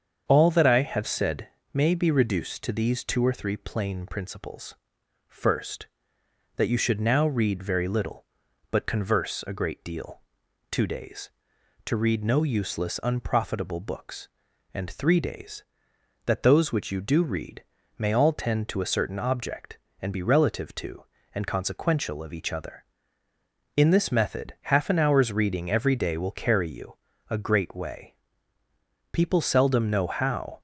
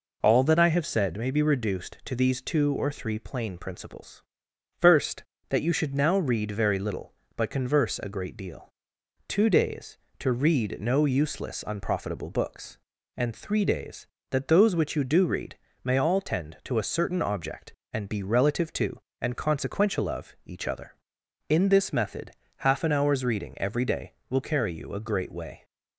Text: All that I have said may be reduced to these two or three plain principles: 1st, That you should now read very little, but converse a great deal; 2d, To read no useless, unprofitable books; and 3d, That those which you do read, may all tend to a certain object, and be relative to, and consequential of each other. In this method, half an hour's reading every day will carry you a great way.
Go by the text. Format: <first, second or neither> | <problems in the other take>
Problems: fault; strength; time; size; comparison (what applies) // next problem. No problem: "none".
second | starts louder than the rest; strong; until 1.2 s; 7 dB // pauses between "said" and "may"; slight; at 1.4 s; 0.26 s long // pauses between "you" and "a"; slight; at 26.9 s; 0.34 s long // goes on to say "People seldom know how"; from 29.1 s on; 1.4 s long